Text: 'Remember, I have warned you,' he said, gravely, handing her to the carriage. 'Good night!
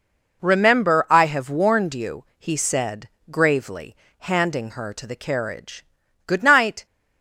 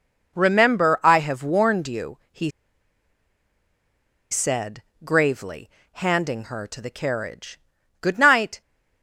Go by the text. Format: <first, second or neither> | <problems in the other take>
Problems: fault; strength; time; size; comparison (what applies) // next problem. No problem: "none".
first | pauses between "he" and "said"; strong; at 2.5 s; 1.8 s long